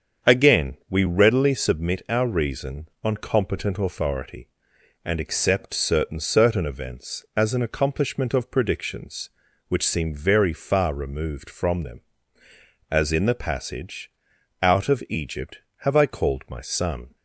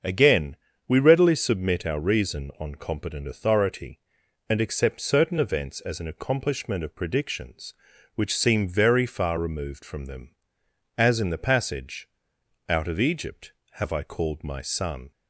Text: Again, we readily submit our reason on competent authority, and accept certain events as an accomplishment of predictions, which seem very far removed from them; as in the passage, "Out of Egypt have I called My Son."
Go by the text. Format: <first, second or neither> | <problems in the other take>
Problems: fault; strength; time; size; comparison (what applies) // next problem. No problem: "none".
second | starts louder than the rest; strong; until 1.3 s; 7.5 dB; also in the second // says "certain" twice; at 6.1 s